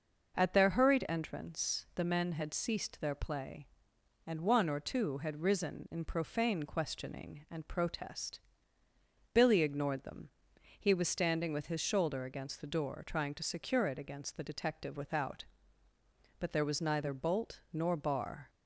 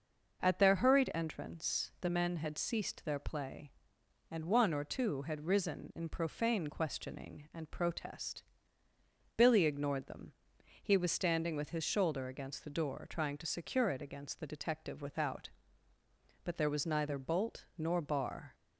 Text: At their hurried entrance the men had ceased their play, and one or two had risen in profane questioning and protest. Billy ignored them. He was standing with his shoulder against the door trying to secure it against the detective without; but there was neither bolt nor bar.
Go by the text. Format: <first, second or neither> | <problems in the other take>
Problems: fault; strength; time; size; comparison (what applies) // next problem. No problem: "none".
neither | none